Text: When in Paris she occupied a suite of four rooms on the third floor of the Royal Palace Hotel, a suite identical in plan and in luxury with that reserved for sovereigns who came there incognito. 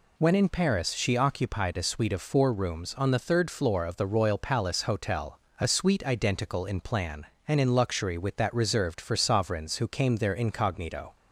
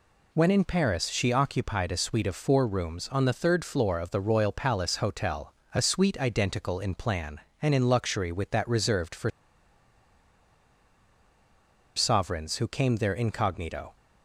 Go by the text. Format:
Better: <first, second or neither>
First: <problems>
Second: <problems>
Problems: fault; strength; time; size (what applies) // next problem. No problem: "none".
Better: first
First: none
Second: pauses between "for" and "sovereigns"; strong; at 9.3 s; 2.6 s long